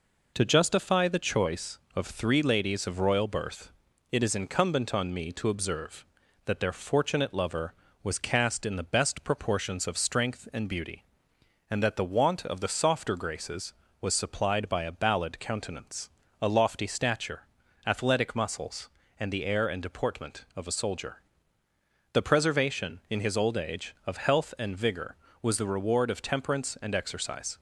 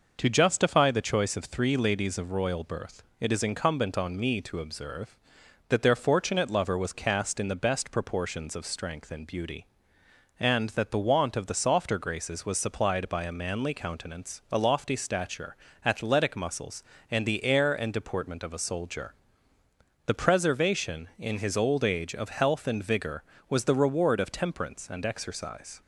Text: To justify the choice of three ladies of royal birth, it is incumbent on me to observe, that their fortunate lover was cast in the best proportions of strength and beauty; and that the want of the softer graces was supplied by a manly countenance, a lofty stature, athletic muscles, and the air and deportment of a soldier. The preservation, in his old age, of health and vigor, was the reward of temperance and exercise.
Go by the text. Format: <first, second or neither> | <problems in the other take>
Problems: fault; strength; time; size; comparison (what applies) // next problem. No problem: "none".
second | says "ballad" for "manly"; at 14.9 s